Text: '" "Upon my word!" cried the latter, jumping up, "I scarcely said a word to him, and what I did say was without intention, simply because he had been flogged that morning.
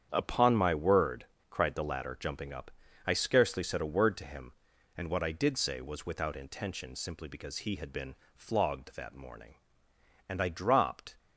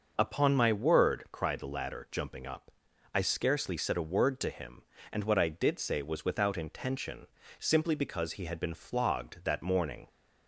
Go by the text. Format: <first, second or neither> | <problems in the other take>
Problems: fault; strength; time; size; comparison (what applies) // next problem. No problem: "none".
second | starts louder than the rest; strong; until 1.1 s; 8.5 dB; noticeable in the second // pauses between "been" and "flogged"; slight; at 8.1 s; 0.20 s long // goes on to say "And I dropped"; noticeable; from 10.2 s on; 0.86 s long